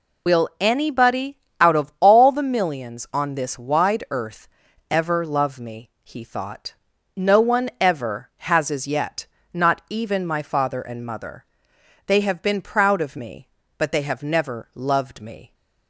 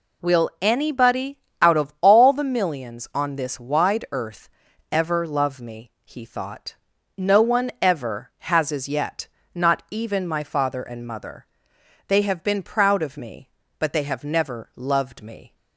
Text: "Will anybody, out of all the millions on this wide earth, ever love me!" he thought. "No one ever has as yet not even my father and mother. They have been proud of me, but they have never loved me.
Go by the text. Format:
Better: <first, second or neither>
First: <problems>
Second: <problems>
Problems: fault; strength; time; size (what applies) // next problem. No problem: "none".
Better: second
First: loses the start of "Will"; at 0.2 s; 60 ms // pauses between "yet" and "not"; slight; at 9.2 s; 0.28 s long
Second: pauses between "yet" and "not"; slight; at 9.2 s; 0.28 s long